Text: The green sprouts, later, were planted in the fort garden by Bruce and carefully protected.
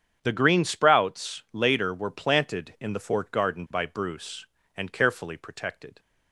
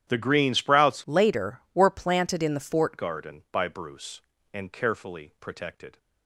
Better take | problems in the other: first | starts louder than the rest; strong; until 1.0 s; 11 dB; strong in the first // changes voice from "later" to "fort"; from 1.0 to 2.9 s; 1.9 s long

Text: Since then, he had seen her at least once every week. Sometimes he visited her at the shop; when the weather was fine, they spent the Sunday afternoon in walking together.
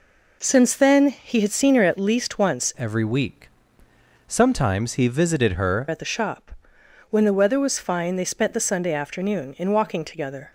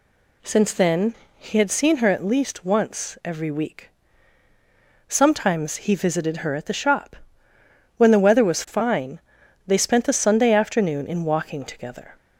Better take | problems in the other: second | changes voice from "every" to "her"; from 2.7 to 5.8 s; 3.1 s long

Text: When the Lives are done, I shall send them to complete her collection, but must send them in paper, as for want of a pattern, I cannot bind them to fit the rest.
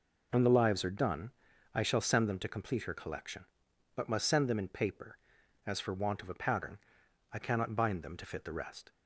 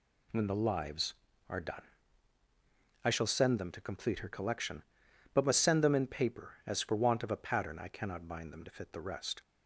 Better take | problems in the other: neither | none

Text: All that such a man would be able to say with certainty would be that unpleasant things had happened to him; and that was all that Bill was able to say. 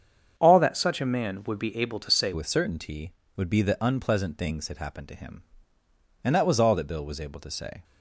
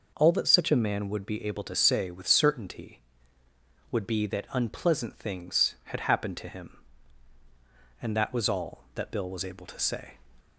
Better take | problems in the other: second | starts louder than the rest; strong; until 1.3 s; 7.5 dB // changes voice at "with"; from 2.3 s on; 5.5 s long

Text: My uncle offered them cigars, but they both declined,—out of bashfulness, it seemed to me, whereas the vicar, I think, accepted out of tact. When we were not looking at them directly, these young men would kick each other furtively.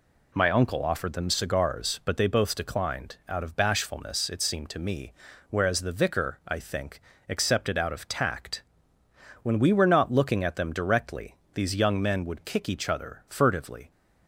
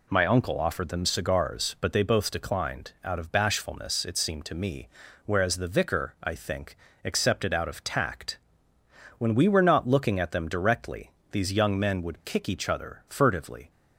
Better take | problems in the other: neither | none

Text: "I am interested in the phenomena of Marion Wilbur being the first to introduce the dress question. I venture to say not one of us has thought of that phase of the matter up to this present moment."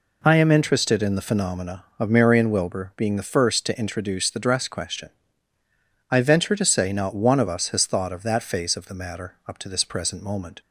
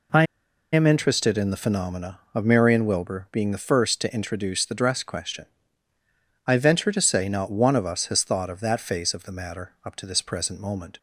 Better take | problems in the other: first | pauses between "I" and "am"; noticeable; at 0.2 s; 0.47 s long

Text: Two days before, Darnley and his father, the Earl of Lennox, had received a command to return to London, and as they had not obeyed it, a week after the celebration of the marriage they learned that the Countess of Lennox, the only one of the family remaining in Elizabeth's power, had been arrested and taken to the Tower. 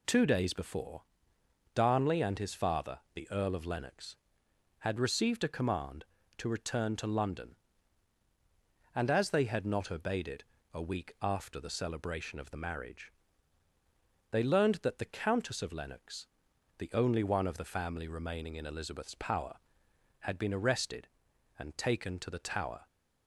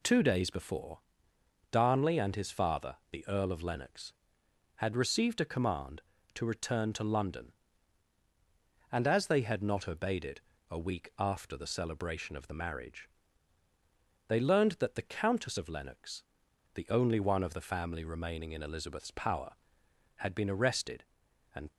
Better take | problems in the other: first | pauses between "marriage" and "they"; at 13.0 s; 1.2 s long; also in the first // stops before "taken to the Tower"; at 21.7 s

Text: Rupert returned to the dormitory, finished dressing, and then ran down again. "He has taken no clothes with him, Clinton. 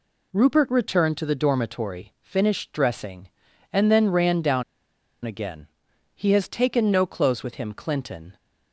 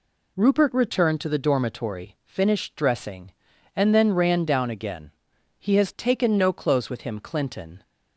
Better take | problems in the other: second | pauses between "down" and "again"; noticeable; at 4.6 s; 0.60 s long

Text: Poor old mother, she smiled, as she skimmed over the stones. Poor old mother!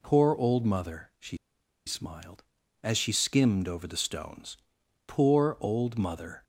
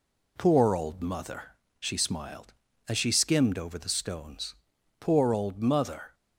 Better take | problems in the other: second | pauses between "she" and "smiled"; noticeable; at 1.3 s; 0.50 s long

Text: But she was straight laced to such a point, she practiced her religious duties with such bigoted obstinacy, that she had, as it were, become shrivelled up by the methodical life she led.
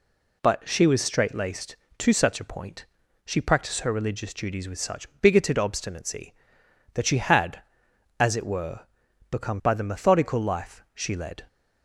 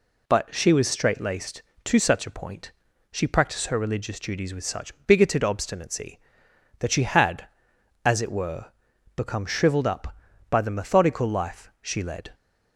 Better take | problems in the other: second | skips "shrivelled up"; at 9.6 s

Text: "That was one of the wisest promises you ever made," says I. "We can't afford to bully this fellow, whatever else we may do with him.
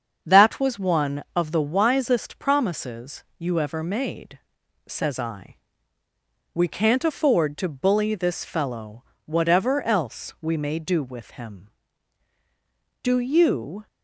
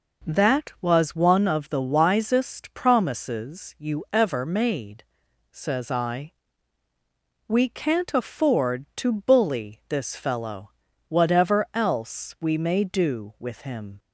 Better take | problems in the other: second | starts louder than the rest; until 1.3 s; 7 dB // pauses between "promises" and "you"; slight; at 3.2 s; 0.16 s long // goes on to say "Do you"; noticeable; from 13.0 s on; 0.86 s long

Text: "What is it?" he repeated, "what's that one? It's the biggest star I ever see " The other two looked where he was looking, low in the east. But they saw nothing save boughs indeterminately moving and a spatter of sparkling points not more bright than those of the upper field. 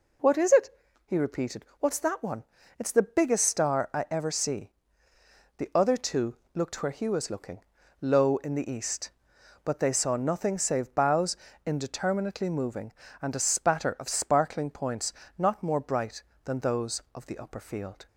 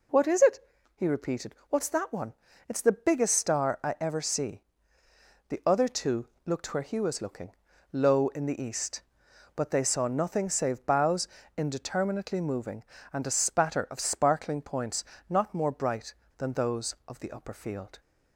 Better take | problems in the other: neither | pauses between "two" and "looked"; slight; the same in both // pauses between "boughs" and "indeterminately"; slight; the same in both // pauses between "points" and "not"; slight; the same in both

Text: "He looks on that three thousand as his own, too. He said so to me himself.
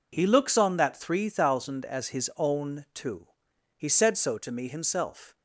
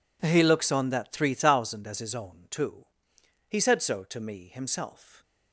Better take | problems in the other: neither | none

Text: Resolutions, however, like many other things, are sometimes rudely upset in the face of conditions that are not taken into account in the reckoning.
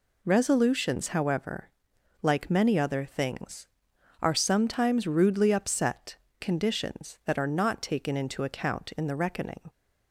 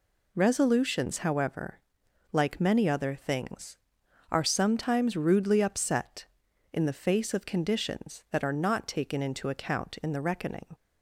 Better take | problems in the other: second | skips "in the face of"; at 6.2 s

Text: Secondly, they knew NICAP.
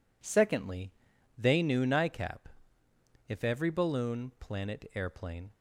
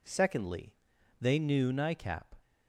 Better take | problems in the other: second | goes on to say "If every balloon planet airplane"; strong; from 3.2 s on; 2.2 s long

